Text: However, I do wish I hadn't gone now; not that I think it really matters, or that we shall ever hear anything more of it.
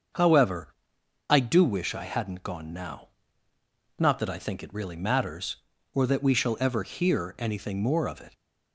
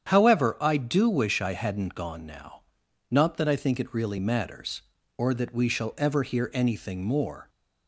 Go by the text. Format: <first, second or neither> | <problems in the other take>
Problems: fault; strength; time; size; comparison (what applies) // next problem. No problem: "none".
first | starts louder than the rest; strong; until 1.1 s; 8.5 dB; also in the first // stops before "of it"; at 7.4 s